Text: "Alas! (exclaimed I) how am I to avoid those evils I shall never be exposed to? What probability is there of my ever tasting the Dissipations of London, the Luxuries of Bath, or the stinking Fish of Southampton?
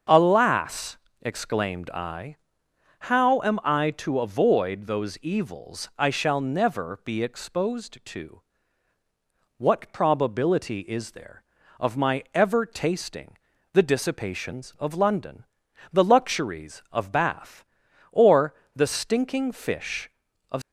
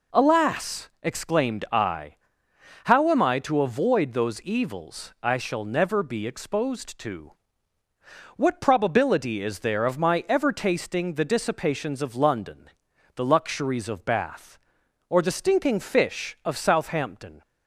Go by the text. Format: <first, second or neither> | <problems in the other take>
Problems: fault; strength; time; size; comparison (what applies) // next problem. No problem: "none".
second | starts louder than the rest; until 1.3 s; 6.5 dB // pauses between "tasting" and "the"; at 13.3 s; 0.38 s long // pauses between "or" and "the"; slight; at 18.5 s; 0.20 s long // stops before "Southampton"; at 20.6 s